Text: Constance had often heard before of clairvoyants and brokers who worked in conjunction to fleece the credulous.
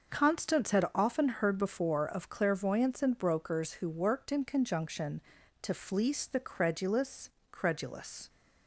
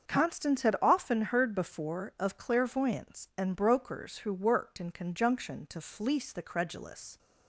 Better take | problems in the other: second | starts louder than the rest; noticeable; until 1.1 s; 6 dB; also in the second // says "credulous" twice; at 7.5 s

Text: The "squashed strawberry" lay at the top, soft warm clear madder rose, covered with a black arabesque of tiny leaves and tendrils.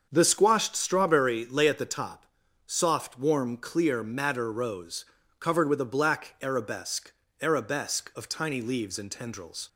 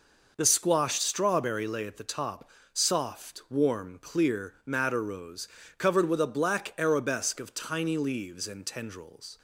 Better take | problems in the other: second | starts louder than the rest; until 1.1 s; 6.5 dB // says "arabesque" twice; at 7.4 s

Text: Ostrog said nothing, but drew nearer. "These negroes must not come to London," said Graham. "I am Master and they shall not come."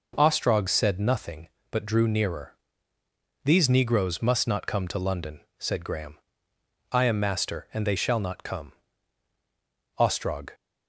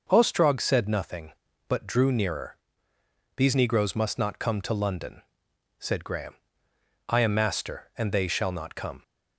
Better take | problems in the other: second | goes on to say "Ostrog"; from 9.9 s on; 0.52 s long

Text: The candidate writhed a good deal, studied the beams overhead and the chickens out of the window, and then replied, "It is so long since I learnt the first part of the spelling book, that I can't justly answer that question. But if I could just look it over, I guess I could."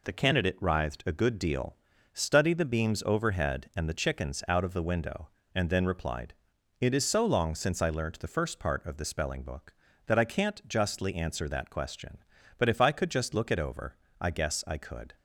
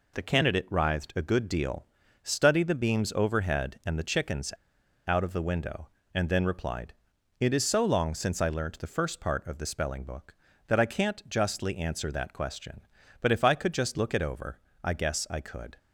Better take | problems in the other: first | pauses between "chickens" and "out"; noticeable; at 4.5 s; 0.54 s long

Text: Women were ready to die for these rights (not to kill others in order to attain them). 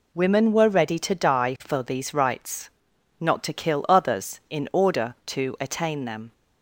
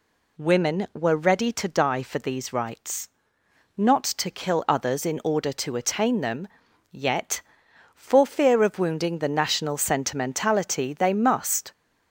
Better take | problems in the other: first | goes on to say "Yet for fear of wounding the national sentimentality they must"; strong; from 6.9 s on; 4.8 s long

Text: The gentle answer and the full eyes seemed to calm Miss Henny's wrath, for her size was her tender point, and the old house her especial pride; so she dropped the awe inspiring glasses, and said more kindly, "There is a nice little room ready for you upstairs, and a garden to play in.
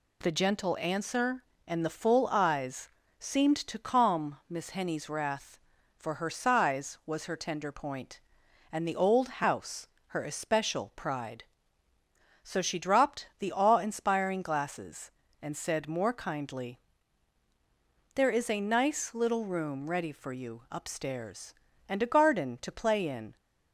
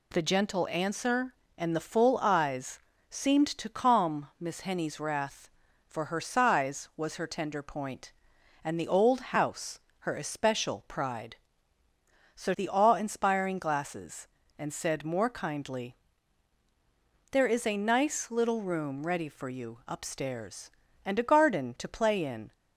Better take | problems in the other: first | pauses between "eyes" and "seemed"; slight; at 2.7 s; 0.30 s long; slight in the first // pauses between "house" and "her"; slight; at 9.7 s; 0.22 s long; slight in the first // skips "she dropped"; at 12.5 s

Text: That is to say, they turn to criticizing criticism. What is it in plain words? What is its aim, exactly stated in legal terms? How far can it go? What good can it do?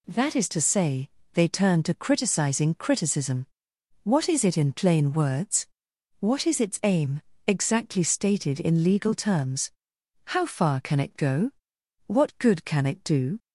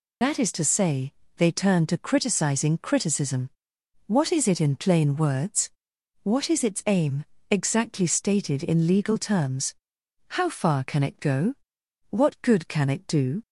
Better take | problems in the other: first | loses the start of "That"; at 0.2 s; 115 ms

